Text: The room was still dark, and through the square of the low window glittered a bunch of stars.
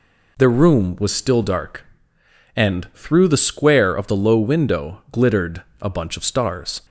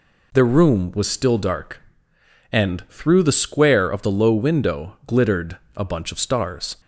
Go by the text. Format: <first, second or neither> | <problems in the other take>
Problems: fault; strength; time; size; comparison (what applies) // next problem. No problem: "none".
neither | pauses between "glittered" and "a"; slight; the same in both